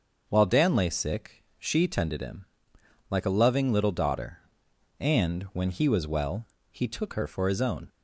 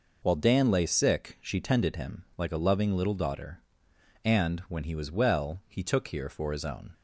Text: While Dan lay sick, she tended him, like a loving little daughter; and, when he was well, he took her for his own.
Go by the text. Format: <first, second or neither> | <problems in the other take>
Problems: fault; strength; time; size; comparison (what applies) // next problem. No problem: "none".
first | says "here" for "her"; at 6.0 s